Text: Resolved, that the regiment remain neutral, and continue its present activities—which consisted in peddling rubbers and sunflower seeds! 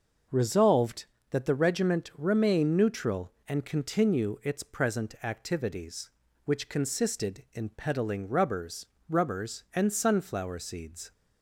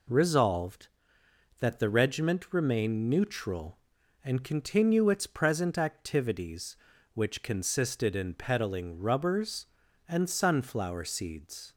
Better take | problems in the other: second | starts louder than the rest; noticeable; until 1.5 s; 6 dB // says "rubbers" twice; at 9.0 s

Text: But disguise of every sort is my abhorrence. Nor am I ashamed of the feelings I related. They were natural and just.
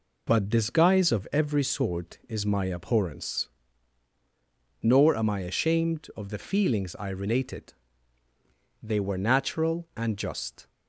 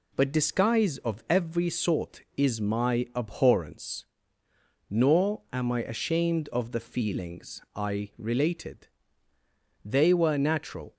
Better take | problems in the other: first | stops before "and just"; at 10.9 s

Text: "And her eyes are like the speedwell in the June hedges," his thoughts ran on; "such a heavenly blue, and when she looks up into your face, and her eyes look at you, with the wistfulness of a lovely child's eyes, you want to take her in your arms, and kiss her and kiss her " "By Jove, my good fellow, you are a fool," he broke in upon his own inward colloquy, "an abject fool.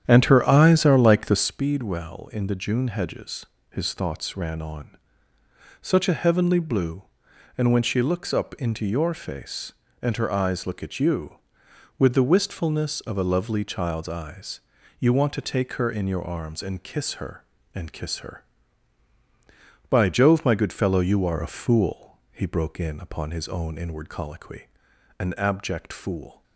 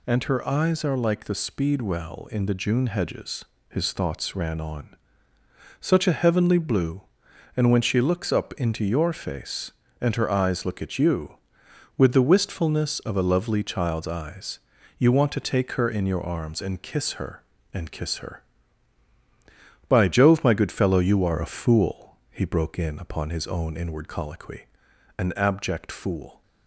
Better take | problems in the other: second | starts louder than the rest; strong; until 1.7 s; 9.5 dB

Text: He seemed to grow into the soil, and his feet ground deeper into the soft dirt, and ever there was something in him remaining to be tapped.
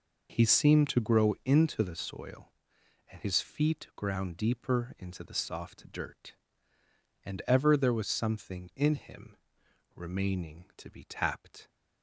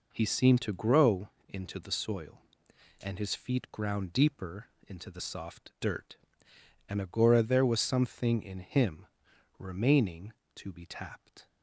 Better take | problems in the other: first | pauses between "grow" and "into"; slight; at 1.2 s; 0.18 s long // pauses between "deeper" and "into"; slight; at 4.6 s; 0.18 s long // says "agora" for "ever"; at 7.0 s // pauses between "him" and "remaining"; noticeable; at 9.0 s; 0.52 s long; noticeable in the first

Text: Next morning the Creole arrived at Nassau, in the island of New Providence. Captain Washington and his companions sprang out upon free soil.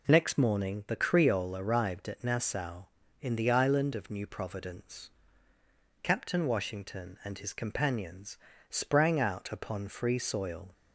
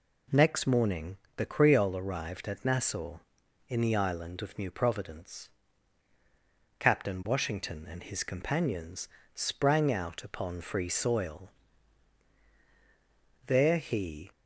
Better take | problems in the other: first | pauses between "morning" and "the"; slight; at 1.1 s; 0.20 s long // pauses between "companions" and "sprang"; slight; at 9.0 s; 0.26 s long; slight in the first // goes on to say "There he"; noticeable; from 13.4 s on; 0.84 s long

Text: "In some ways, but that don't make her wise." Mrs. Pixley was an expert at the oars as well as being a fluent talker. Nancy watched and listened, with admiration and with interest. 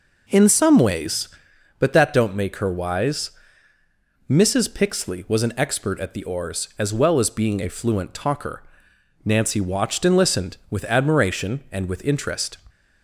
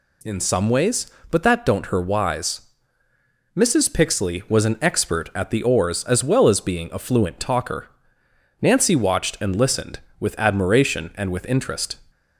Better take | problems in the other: first | skips "make"; at 1.8 s

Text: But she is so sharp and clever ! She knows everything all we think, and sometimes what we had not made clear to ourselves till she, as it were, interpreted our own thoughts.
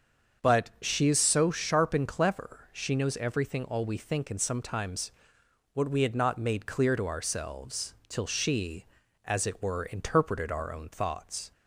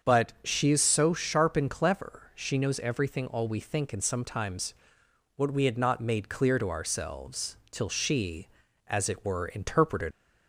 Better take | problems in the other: first | starts louder than the rest; until 1.1 s; 7 dB; also in the first // pauses between "sometimes" and "what"; noticeable; at 4.7 s; 0.62 s long; noticeable in the first // stops before "our own thoughts"; at 10.1 s

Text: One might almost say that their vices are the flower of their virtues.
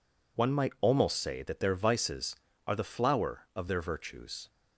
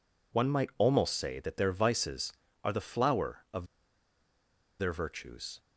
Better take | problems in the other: first | pauses between "of" and "their"; at 3.6 s; 1.1 s long

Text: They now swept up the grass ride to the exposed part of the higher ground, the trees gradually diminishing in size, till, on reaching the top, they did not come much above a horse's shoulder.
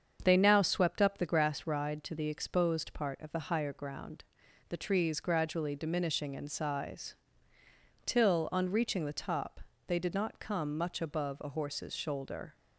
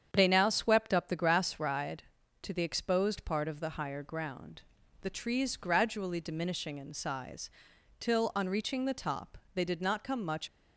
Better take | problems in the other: first | starts louder than the rest; strong; until 1.1 s; 8 dB; strong in the first // stops before "above a horse's shoulder"; at 10.4 s

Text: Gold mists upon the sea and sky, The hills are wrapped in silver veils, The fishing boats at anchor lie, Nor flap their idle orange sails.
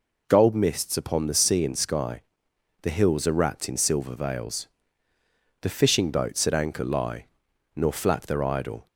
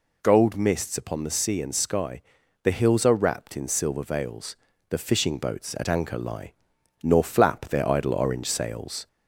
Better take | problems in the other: second | stops before "orange sails"; at 8.8 s

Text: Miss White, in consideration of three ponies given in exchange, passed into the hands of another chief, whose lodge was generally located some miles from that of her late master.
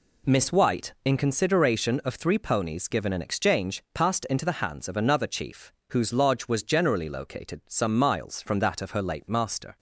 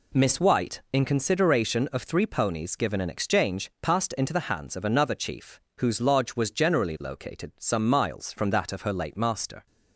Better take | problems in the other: neither | none

